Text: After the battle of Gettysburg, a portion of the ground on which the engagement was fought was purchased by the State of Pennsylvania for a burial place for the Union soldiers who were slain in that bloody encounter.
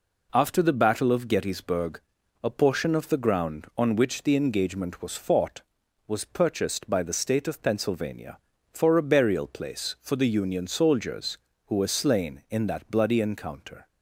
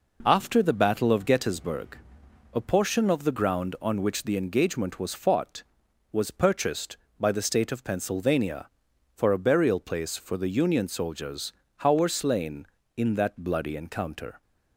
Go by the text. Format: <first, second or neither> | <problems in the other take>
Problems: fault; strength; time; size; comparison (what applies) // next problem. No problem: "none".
first | says "how" for "who"; at 11.7 s